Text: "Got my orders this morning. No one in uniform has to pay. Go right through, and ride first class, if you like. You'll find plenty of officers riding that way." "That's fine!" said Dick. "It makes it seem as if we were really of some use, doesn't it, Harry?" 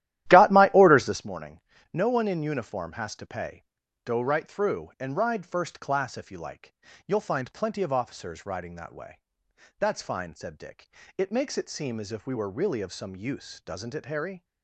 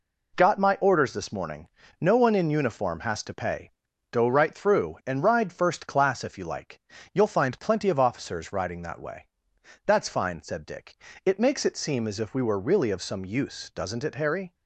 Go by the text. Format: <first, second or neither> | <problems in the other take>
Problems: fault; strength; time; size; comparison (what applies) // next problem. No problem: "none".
second | starts louder than the rest; strong; until 1.2 s; 13 dB